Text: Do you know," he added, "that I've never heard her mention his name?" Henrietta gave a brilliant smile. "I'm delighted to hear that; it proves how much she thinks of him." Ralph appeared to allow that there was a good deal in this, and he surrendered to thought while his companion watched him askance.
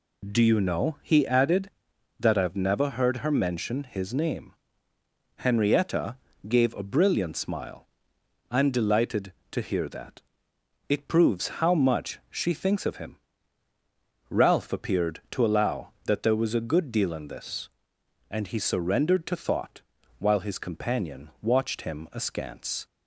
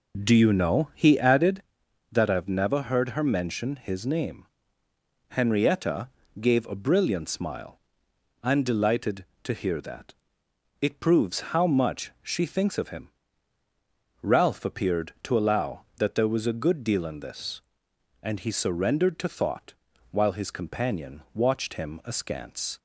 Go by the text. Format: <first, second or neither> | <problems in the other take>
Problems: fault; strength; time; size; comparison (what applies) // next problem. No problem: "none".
first | starts louder than the rest; noticeable; until 1.6 s; 4.5 dB // pauses between "Henrietta" and "gave"; slight; at 6.0 s; 0.32 s long; slight in the first // pauses between "thought" and "while"; at 19.7 s; 0.38 s long; also in the first